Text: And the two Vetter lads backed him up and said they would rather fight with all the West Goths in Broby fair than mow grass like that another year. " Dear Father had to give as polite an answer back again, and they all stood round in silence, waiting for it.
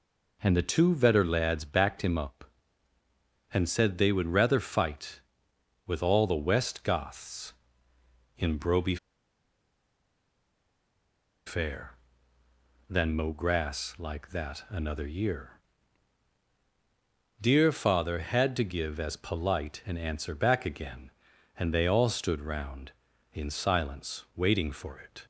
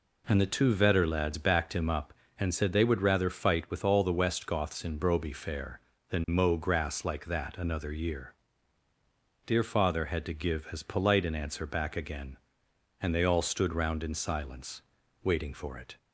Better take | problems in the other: second | pauses between "Broby" and "fair"; strong; at 8.9 s; 2.5 s long

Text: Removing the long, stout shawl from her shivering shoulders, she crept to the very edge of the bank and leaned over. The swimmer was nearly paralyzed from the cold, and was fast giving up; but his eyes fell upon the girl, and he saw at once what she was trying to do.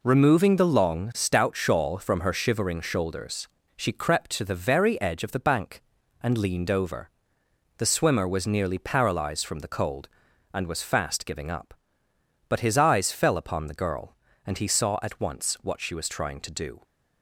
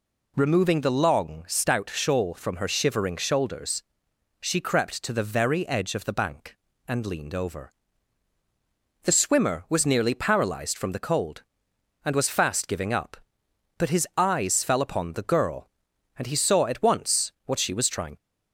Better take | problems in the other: first | pauses between "once" and "what"; slight; at 17.3 s; 0.16 s long // stops before "to do"; at 18.1 s

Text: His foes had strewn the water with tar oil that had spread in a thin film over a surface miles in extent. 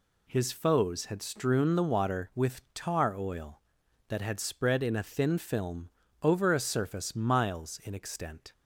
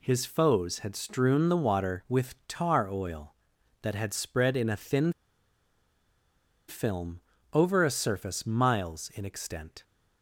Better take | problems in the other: first | pauses between "thin" and "film"; strong; at 5.1 s; 1.5 s long // pauses between "film" and "over"; slight; at 7.1 s; 0.32 s long; slight in the first

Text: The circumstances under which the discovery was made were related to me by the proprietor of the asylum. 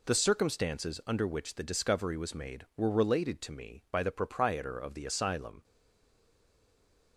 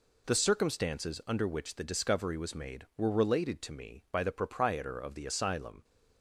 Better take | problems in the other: second | stays silent after the last word; noticeable; from 5.6 s on; 1.5 s long

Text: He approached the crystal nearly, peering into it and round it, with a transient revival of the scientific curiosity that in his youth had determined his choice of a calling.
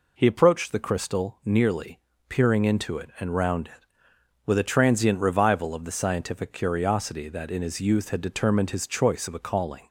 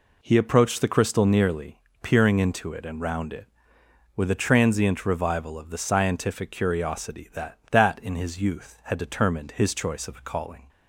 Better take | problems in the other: first | says "that" twice; at 7.7 s

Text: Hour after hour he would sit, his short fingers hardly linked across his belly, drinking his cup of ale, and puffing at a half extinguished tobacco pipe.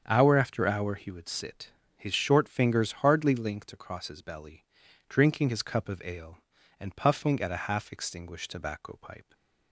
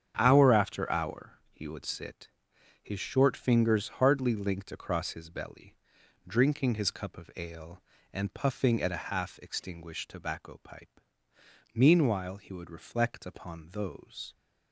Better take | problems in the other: first | starts louder than the rest; strong; until 1.1 s; 8 dB; strong in the first // goes on to say "Meanwhile he would reflect upon those"; strong; from 11.7 s on; 2.6 s long

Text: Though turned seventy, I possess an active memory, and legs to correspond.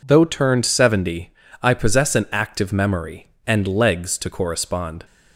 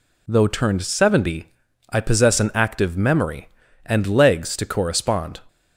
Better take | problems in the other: neither | none

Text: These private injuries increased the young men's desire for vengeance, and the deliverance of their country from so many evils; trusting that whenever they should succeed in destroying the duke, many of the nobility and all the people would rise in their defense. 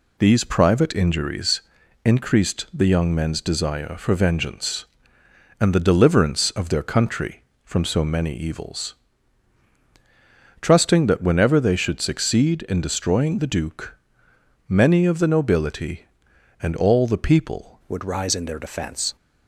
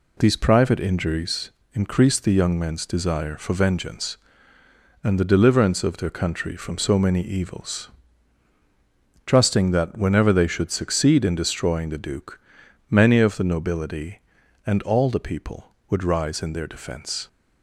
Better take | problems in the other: second | pauses between "injuries" and "increased"; at 1.6 s; 0.42 s long; slight in the second // changes voice at "would"; from 17.8 s on; 1.3 s long

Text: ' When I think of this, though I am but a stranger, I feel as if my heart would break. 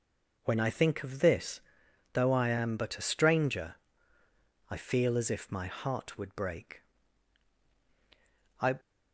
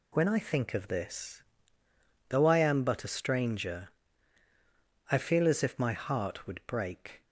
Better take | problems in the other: second | goes on to say "I"; slight; from 8.6 s on; 0.18 s long

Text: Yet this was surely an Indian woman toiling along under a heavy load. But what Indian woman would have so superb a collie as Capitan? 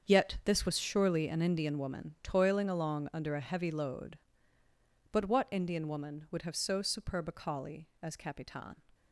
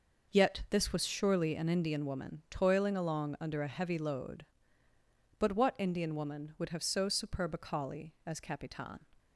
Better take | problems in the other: second | gets quieter; strong; throughout; 12.5 dB

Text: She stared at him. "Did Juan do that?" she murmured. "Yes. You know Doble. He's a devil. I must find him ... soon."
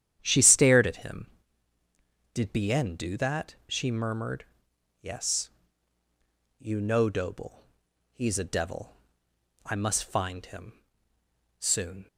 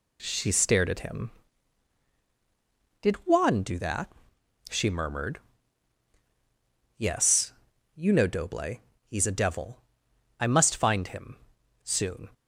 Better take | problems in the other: second | starts louder than the rest; strong; until 1.2 s; 10 dB // says "Bien" for "Juan"; at 2.5 s

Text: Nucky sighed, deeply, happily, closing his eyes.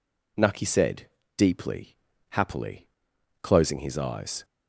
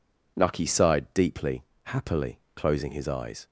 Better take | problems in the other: second | says "said" for "sighed"; at 0.6 s

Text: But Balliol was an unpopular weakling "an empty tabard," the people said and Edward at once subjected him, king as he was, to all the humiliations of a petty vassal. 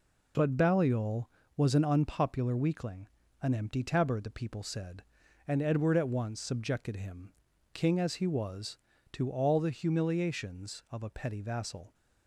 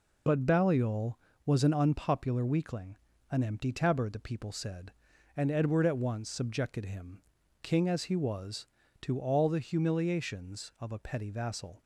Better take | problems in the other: first | loses the start of "But"; at 0.2 s; 20 ms // pauses between "weakling" and "an"; slight; at 2.9 s; 0.32 s long; slight in the first

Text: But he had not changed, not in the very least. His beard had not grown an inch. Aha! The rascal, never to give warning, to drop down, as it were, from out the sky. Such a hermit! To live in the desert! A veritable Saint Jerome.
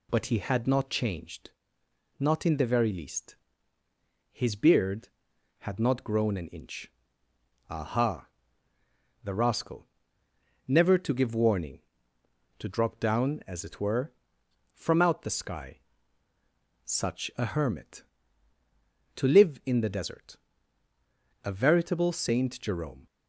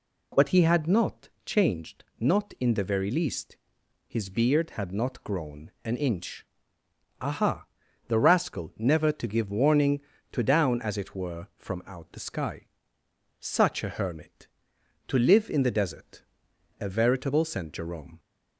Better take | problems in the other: first | pauses between "not" and "changed"; slight; at 1.2 s; 0.16 s long // skips "drop"; at 10.4 s

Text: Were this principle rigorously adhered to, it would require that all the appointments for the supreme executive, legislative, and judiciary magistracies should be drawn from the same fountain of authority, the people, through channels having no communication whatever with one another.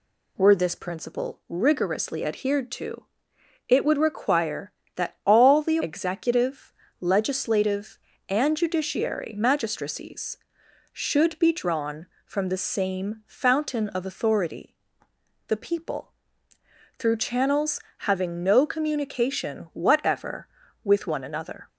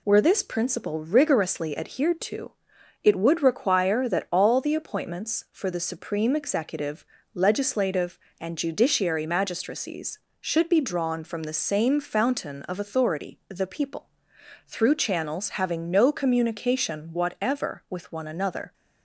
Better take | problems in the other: second | skips "appointments for the supreme"; at 5.7 s // pauses between "channels" and "having"; slight; at 17.7 s; 0.18 s long

